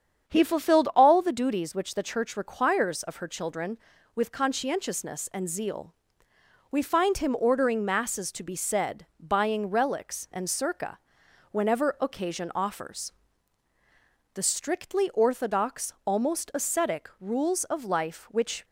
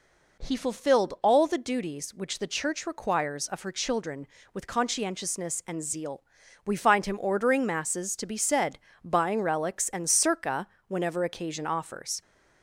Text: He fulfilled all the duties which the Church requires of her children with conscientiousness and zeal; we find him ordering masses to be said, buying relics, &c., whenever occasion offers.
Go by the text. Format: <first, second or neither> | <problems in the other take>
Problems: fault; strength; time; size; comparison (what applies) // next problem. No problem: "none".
second | starts louder than the rest; strong; until 1.3 s; 8 dB // goes on to say "The strictly orthodox almost ascetic rules of life which"; strong; from 14.3 s on; 4.3 s long